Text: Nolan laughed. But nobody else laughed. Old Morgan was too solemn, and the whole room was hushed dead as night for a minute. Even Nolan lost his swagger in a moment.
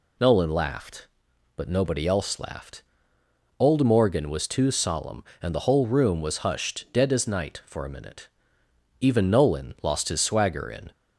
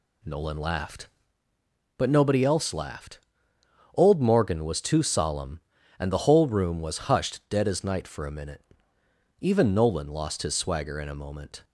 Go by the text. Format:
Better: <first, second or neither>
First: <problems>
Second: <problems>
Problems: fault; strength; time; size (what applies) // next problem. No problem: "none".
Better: second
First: stops before "a moment"; at 10.9 s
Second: none